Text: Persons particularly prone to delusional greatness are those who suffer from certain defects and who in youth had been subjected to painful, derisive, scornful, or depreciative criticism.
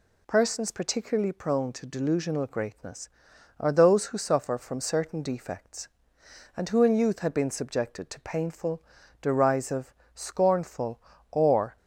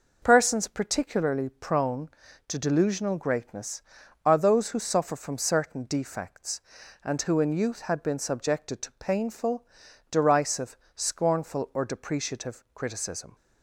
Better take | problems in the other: second | stops before "depreciative criticism"; at 11.7 s

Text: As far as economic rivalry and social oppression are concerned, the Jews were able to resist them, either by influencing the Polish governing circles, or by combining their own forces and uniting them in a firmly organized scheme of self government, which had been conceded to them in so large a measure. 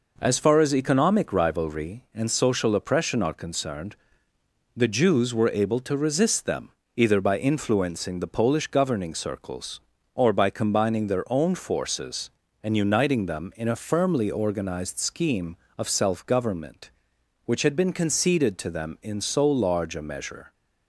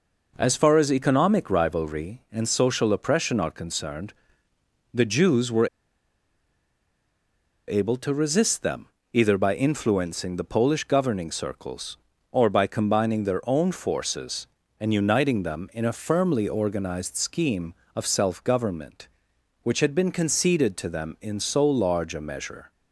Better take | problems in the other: first | pauses between "were" and "able"; strong; at 5.6 s; 1.9 s long

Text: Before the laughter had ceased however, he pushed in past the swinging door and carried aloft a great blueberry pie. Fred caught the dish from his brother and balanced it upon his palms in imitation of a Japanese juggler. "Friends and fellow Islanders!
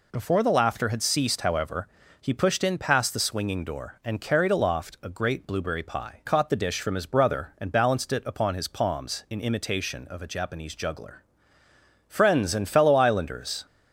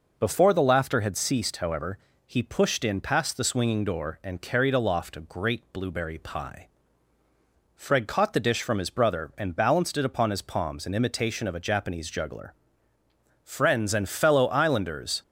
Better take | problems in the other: second | skips "Fred"; at 6.2 s

